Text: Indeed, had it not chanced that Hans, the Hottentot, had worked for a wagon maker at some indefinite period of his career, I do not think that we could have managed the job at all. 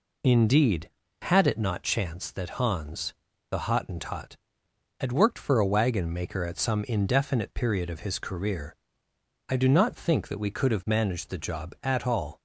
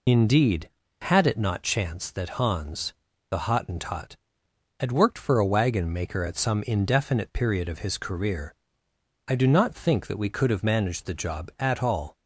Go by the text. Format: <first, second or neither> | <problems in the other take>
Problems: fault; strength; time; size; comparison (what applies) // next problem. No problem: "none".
first | loses the start of "Indeed"; at 0.0 s; 40 ms